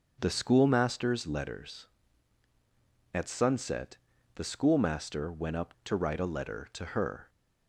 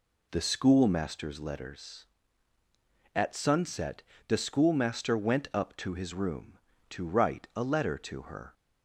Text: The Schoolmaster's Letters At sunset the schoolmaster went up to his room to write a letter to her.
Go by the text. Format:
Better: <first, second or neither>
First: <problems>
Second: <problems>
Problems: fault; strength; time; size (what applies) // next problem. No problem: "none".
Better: second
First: starts louder than the rest; until 1.2 s; 6.5 dB // pauses between "sunset" and "the"; at 3.9 s; 0.40 s long // skips "to his room"; at 5.7 s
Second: pauses between "sunset" and "the"; slight; at 4.0 s; 0.24 s long